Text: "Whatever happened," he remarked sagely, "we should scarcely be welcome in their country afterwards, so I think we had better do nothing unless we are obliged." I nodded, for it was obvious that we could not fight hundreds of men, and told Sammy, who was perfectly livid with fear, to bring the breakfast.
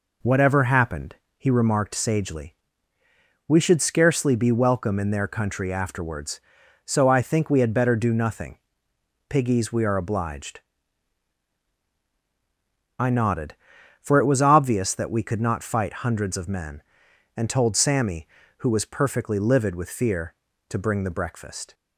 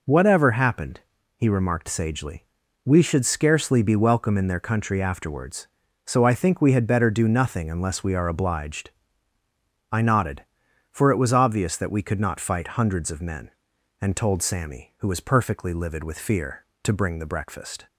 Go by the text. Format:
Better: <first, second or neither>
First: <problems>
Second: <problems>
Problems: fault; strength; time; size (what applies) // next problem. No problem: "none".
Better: second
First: says "piggies" for "unless"; at 9.2 s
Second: none